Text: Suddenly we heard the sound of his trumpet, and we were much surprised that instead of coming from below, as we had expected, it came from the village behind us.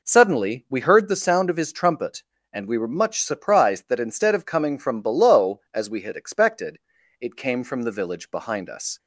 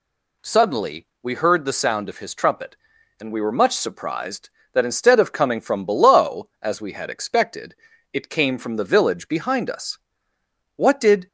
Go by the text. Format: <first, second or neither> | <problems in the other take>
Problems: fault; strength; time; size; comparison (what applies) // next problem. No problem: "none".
first | pauses between "Suddenly" and "we"; slight; at 1.0 s; 0.16 s long // goes on to say "What did"; from 10.7 s on; 0.52 s long